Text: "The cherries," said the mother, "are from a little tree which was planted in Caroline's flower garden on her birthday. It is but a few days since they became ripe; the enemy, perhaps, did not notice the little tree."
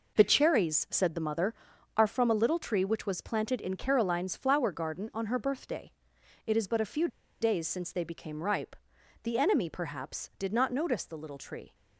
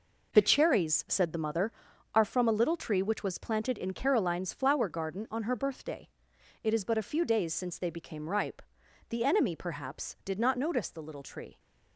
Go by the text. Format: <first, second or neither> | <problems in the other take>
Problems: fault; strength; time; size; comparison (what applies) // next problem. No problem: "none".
second | pauses between "few" and "days"; slight; at 7.0 s; 0.33 s long